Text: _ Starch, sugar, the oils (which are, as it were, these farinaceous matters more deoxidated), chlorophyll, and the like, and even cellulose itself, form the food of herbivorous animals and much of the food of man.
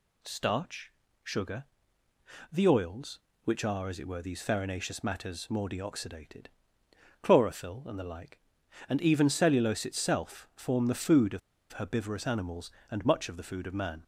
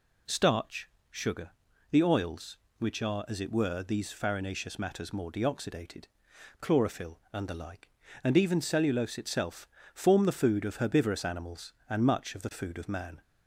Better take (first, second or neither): second